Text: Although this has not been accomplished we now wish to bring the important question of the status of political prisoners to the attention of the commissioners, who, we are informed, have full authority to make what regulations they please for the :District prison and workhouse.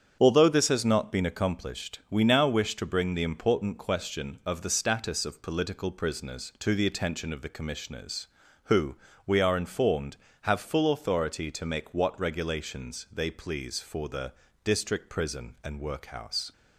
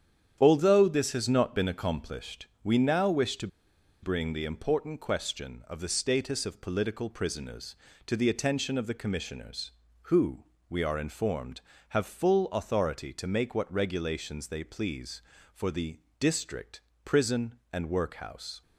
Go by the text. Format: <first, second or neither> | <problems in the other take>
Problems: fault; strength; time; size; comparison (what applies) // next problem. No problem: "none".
first | starts louder than the rest; strong; until 1.4 s; 9 dB; strong in the first // pauses between "accomplished" and "we"; slight; at 2.4 s; 0.16 s long // pauses between "to" and "bring"; noticeable; at 3.4 s; 0.55 s long // pauses between "District" and "prison"; slight; at 16.8 s; 0.22 s long